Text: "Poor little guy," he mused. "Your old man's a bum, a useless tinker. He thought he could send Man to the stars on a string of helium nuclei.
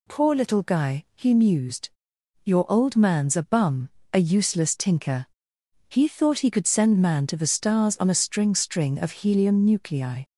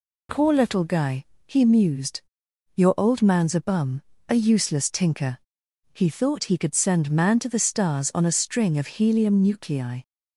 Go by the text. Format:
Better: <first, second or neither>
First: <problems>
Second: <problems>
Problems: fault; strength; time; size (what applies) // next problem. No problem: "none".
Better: second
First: says "string" twice; at 8.5 s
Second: none